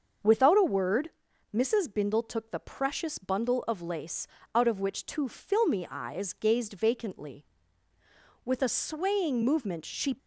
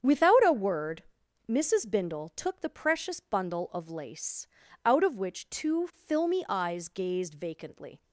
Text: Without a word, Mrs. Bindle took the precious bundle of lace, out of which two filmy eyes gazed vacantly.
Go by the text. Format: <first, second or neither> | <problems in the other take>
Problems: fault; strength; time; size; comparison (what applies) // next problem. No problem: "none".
second | starts louder than the rest; until 1.6 s; 6.5 dB; strong in the second // goes on to say "With a swaying movement she"; strong; from 8.4 s on; 1.7 s long